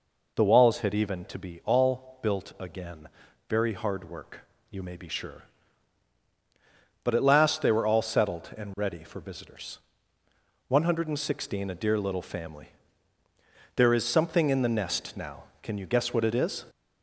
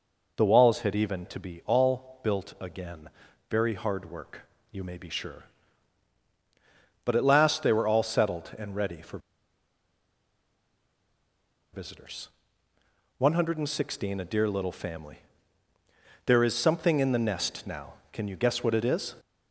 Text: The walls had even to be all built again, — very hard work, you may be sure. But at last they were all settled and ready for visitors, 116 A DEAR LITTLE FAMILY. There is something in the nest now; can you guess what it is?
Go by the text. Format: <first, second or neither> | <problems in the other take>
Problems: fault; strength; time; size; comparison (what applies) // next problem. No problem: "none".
first | pauses between "for" and "visitors"; strong; at 9.1 s; 2.5 s long